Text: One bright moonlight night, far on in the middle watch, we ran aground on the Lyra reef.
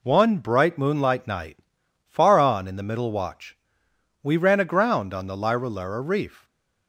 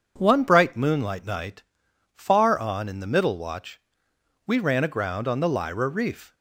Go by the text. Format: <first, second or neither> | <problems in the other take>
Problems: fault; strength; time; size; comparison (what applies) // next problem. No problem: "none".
second | says "Lyra" twice; at 5.6 s // stays silent after the last word; slight; from 6.3 s on; 0.5 s long